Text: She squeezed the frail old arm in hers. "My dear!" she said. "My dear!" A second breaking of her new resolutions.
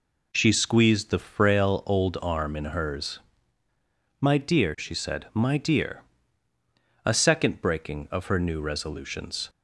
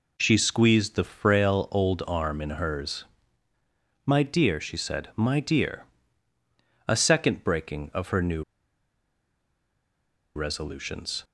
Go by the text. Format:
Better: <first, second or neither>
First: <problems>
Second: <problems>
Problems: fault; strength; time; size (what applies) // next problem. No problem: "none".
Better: first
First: none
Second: pauses between "new" and "resolutions"; strong; at 8.4 s; 1.9 s long